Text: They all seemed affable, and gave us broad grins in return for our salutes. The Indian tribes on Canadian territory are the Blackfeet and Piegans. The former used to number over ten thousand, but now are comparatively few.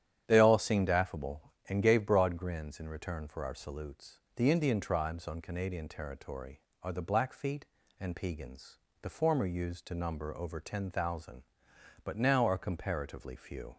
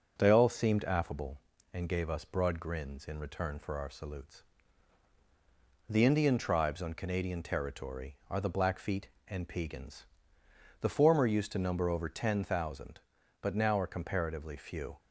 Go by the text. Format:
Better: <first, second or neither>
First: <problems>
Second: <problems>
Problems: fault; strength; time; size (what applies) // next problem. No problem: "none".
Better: second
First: starts louder than the rest; strong; until 1.2 s; 9.5 dB // skips "us"; at 2.0 s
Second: starts louder than the rest; until 1.1 s; 7 dB